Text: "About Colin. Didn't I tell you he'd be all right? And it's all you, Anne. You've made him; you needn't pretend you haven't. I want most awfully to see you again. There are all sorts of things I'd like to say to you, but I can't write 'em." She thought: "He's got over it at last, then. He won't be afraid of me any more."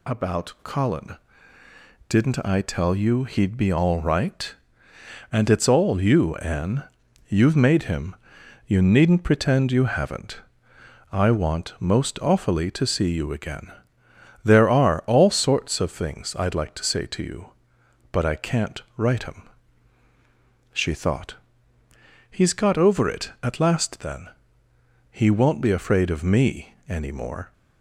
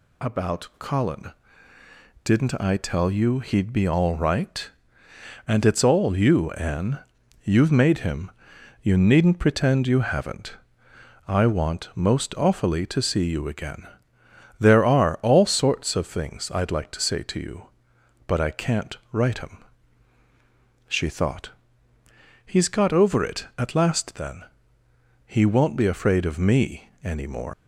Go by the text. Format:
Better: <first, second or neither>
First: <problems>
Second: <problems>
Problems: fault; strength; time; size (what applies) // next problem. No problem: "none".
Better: first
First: none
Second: leaves "more" unfinished; at 27.5 s; 140 ms